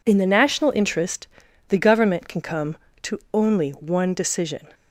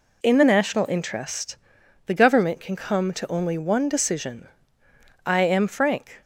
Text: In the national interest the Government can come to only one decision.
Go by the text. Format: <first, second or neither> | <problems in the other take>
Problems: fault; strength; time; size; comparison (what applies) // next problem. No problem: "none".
first | pauses between "interest" and "the"; noticeable; at 1.5 s; 0.52 s long; also in the first // goes on to say "I am frank"; noticeable; from 5.2 s on; 0.96 s long